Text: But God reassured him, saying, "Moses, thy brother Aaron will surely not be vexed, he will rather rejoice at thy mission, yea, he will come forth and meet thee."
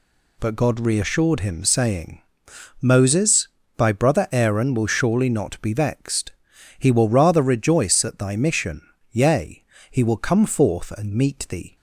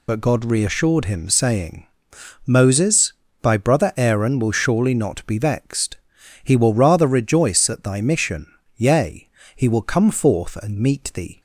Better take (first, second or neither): first